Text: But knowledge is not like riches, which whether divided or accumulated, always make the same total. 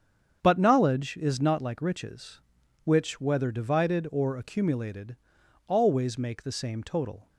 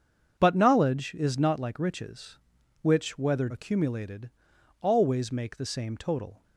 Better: first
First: starts louder than the rest; strong; until 1.4 s; 7.5 dB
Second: starts louder than the rest; strong; until 1.4 s; 7 dB // skips "divided or"; at 3.4 s

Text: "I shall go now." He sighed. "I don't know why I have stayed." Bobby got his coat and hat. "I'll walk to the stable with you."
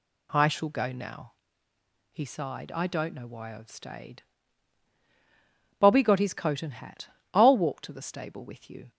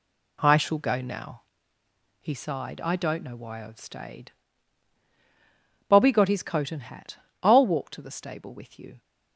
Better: first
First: none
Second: gets quieter; strong; throughout; 7.5 dB

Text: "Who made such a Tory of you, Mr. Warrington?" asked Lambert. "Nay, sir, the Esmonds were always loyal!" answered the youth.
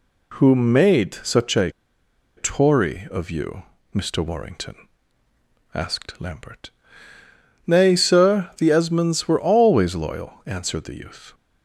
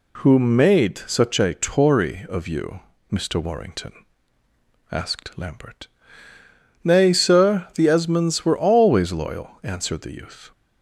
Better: second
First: pauses between "a" and "Tory"; noticeable; at 1.7 s; 0.66 s long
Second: none

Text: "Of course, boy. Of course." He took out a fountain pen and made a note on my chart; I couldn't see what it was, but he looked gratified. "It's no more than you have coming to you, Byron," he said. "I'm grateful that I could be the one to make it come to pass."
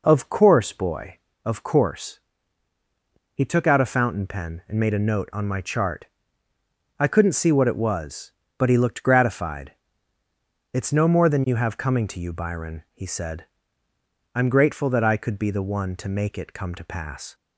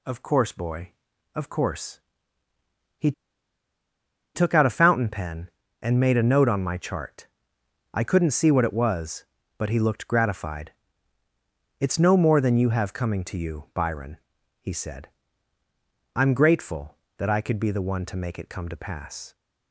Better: first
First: none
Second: pauses between "He" and "took"; at 3.1 s; 1.2 s long

